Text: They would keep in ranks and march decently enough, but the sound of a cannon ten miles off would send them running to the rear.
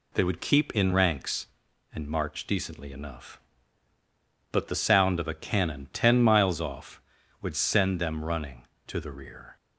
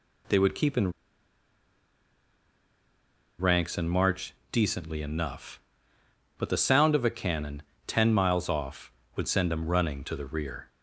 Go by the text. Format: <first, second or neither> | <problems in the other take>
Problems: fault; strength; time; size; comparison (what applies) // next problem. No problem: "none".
first | pauses between "in" and "ranks"; strong; at 0.9 s; 2.4 s long // pauses between "march" and "decently"; slight; at 4.3 s; 0.18 s long // pauses between "cannon" and "ten"; slight; at 7.6 s; 0.26 s long